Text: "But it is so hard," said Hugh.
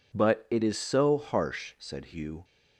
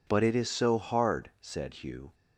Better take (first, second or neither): second